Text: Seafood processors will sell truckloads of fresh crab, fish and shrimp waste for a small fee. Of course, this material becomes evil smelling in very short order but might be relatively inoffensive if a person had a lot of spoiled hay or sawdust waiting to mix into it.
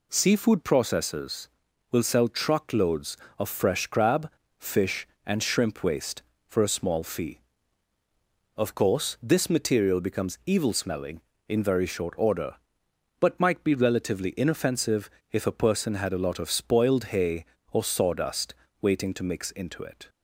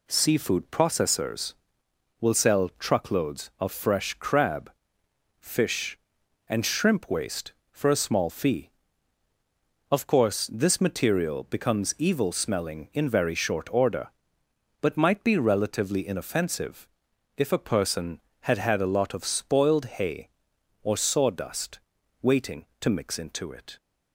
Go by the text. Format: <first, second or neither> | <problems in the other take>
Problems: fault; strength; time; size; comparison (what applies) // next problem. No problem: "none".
first | pauses between "inoffensive" and "if"; noticeable; at 16.8 s; 0.48 s long; slight in the first // says "had" twice; at 18.5 s // pauses between "sawdust" and "waiting"; at 21.7 s; 0.42 s long; slight in the first